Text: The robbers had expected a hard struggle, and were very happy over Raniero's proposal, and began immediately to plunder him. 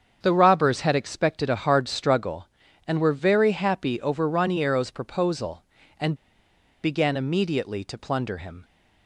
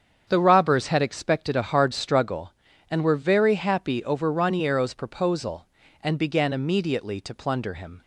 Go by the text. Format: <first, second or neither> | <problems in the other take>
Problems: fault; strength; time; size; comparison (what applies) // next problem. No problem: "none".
second | starts louder than the rest; strong; until 1.2 s; 7 dB; strong in the second // pauses between "and" and "began"; noticeable; at 6.1 s; 0.69 s long